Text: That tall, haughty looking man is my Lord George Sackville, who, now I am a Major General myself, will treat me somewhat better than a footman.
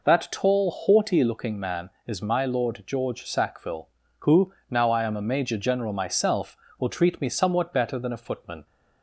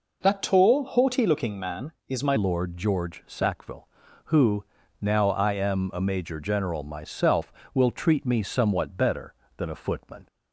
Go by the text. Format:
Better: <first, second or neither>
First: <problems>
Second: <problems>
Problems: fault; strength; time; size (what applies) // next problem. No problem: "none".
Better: first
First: none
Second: changes voice at "Lord"; from 2.3 s on; 7.9 s long